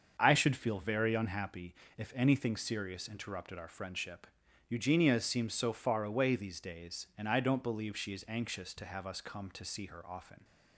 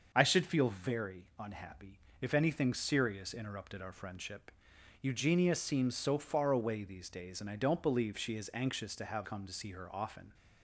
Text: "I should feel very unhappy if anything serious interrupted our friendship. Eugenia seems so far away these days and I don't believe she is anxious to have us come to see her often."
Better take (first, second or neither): first